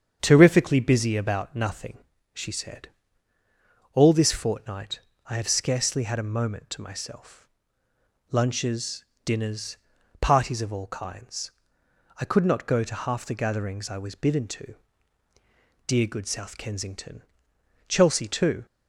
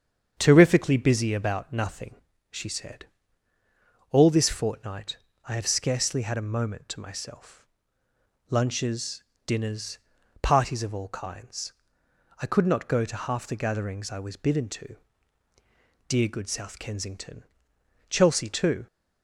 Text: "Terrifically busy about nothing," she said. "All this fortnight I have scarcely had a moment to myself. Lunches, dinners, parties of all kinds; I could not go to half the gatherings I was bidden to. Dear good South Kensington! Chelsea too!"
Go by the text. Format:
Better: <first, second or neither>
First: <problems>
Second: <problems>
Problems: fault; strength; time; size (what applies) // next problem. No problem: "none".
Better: neither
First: starts louder than the rest; strong; until 1.2 s; 8 dB // pauses between "fortnight" and "I"; slight; at 5.0 s; 0.26 s long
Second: starts louder than the rest; strong; until 1.3 s; 8 dB // pauses between "fortnight" and "I"; slight; at 5.1 s; 0.28 s long